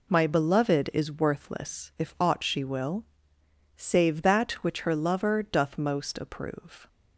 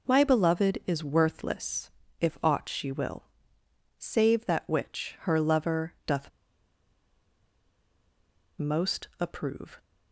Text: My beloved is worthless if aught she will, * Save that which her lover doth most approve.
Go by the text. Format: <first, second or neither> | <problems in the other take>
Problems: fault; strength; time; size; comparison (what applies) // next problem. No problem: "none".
first | pauses between "worthless" and "if"; slight; at 1.9 s; 0.30 s long // pauses between "doth" and "most"; strong; at 6.2 s; 2.2 s long